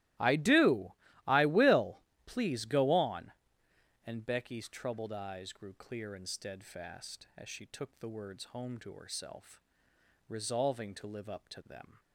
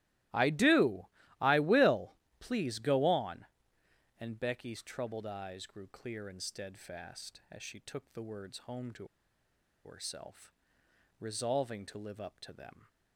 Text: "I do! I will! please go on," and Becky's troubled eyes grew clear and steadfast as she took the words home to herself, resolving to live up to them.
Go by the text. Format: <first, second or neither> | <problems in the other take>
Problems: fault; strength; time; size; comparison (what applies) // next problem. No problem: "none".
first | starts louder than the rest; strong; until 1.6 s; 16.5 dB; strong in the first // pauses between "to" and "herself"; noticeable; at 9.0 s; 0.79 s long